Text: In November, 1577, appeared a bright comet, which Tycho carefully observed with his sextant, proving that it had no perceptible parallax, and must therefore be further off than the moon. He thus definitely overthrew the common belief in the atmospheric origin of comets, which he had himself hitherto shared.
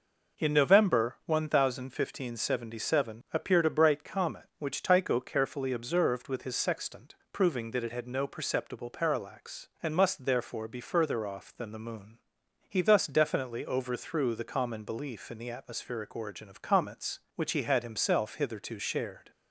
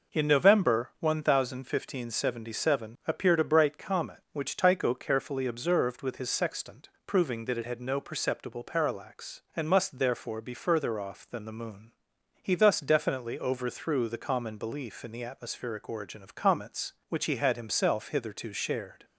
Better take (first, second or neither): neither